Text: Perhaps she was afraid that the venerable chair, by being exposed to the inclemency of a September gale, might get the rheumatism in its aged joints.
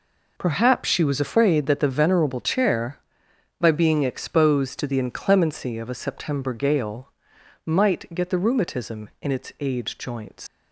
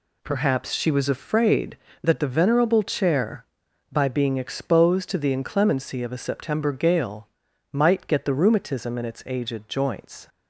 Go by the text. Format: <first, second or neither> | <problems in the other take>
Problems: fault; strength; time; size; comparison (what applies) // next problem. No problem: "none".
second | leaves "joints" unfinished; at 10.4 s; 85 ms